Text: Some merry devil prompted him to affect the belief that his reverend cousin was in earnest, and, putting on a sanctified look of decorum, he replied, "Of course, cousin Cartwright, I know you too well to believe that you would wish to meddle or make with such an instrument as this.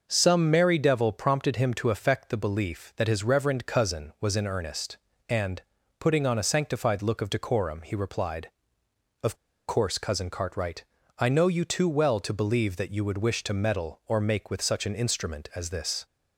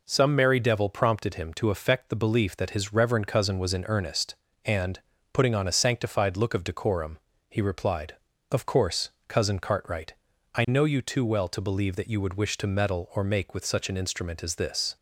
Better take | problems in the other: second | starts louder than the rest; noticeable; until 1.0 s; 6 dB // pauses between "Of" and "course"; slight; at 9.3 s; 0.33 s long

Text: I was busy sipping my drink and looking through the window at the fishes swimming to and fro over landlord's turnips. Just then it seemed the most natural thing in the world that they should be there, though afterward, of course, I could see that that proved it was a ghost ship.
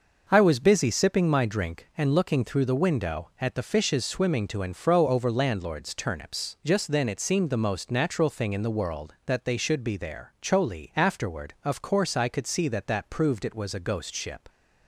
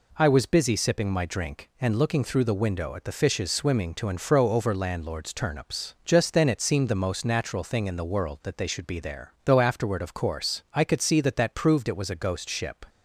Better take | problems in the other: second | says "choli" for "though"; at 10.4 s

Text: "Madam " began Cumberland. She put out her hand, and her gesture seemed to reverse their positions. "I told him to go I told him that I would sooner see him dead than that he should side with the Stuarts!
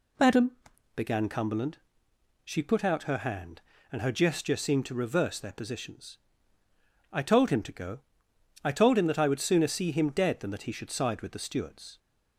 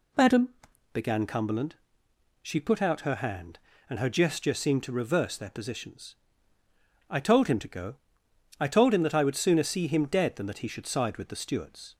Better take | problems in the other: neither | pauses between "go" and "I"; noticeable; the same in both

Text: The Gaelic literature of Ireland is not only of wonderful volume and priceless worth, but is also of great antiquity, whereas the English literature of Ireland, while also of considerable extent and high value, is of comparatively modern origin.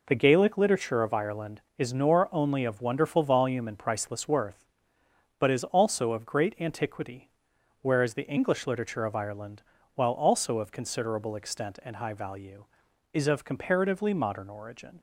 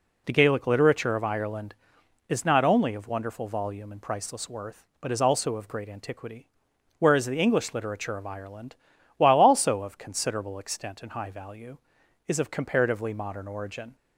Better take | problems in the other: second | says "nor" for "not"; at 1.9 s

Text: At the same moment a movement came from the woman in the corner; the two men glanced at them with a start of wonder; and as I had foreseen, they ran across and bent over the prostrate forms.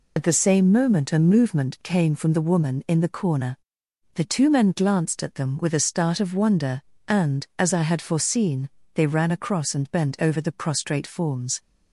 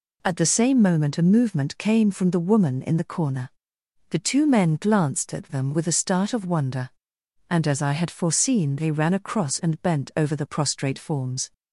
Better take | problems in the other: second | loses the start of "At"; at 0.1 s; 70 ms

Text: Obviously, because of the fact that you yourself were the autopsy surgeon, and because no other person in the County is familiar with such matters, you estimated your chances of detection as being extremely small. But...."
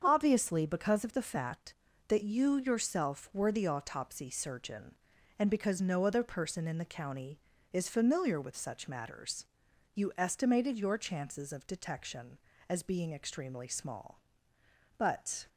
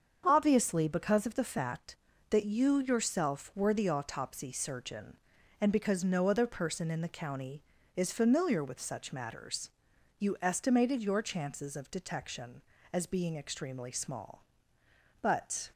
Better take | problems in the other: neither | starts louder than the rest; strong; the same in both

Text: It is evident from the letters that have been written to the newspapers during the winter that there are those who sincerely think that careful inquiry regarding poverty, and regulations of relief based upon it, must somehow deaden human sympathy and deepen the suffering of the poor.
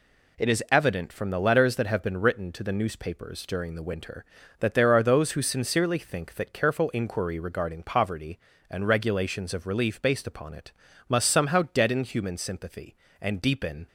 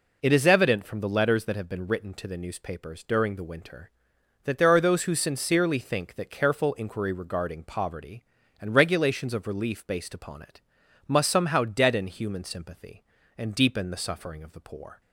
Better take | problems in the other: second | stops before "the suffering of the poor"; at 13.8 s

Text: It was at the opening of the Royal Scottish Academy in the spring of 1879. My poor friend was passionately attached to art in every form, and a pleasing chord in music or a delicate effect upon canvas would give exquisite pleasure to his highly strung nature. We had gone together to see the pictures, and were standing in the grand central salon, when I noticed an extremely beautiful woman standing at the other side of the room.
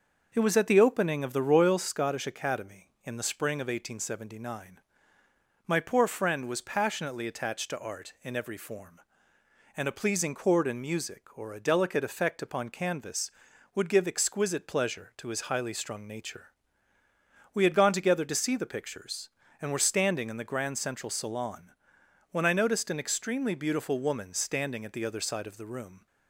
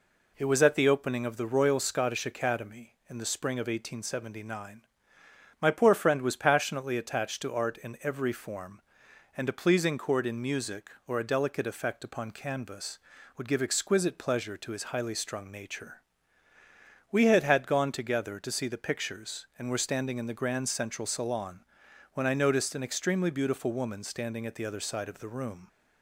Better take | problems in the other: first | says "had" twice; at 17.4 s

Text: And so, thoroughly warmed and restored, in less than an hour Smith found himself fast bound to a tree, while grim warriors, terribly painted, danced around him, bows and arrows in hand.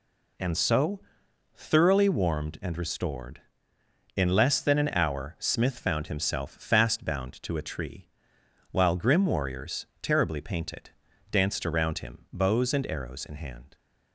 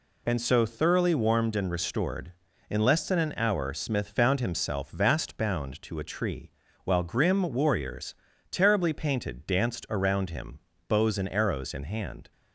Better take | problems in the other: first | says "vast" for "fast"; at 4.8 s

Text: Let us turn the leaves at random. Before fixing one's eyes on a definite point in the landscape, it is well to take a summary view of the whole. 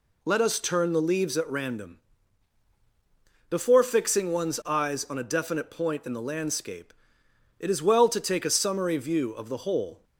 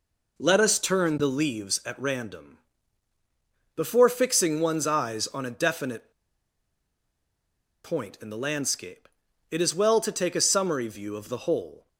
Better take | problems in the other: first | pauses between "definite" and "point"; strong; at 6.1 s; 1.7 s long

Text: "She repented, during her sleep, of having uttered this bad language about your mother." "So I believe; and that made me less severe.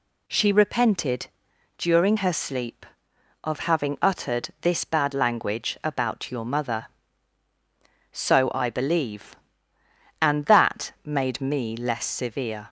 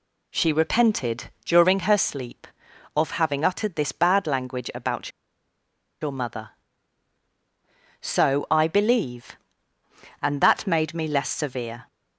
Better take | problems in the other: first | pauses between "about" and "your"; noticeable; at 5.1 s; 0.90 s long

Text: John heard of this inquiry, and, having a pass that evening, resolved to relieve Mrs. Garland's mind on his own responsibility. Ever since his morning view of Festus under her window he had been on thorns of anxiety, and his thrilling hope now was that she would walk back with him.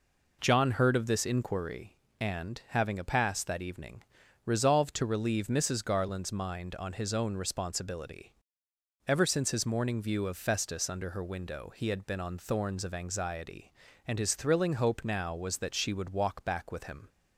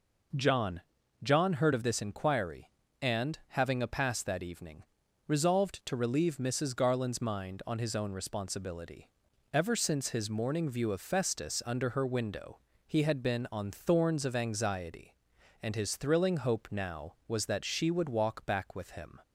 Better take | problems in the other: first | says "John" twice; at 1.2 s // pauses between "window" and "he"; slight; at 12.5 s; 0.26 s long

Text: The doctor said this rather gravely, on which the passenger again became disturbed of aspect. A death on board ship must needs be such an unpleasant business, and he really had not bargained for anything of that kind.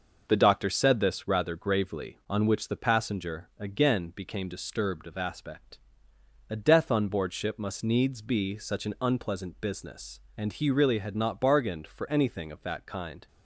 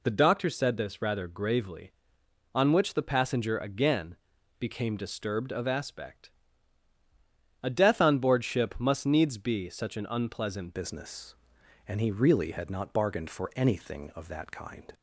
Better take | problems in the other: first | pauses between "again" and "became"; at 4.1 s; 0.42 s long // changes voice at "business"; from 10.7 s on; 4.2 s long

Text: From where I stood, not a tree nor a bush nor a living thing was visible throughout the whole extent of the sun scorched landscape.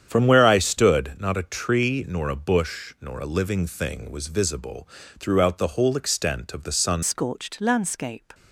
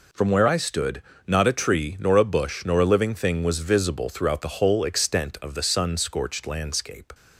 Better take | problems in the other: second | starts louder than the rest; strong; until 1.1 s; 8.5 dB // pauses between "visible" and "throughout"; slight; at 4.8 s; 0.32 s long // changes voice at "scorched"; from 7.0 s on; 1.3 s long

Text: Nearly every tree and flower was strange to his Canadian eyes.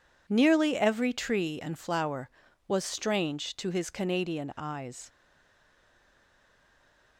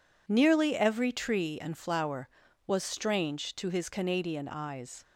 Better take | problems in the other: second | stays silent after the last word; noticeable; from 5.0 s on; 2.1 s long

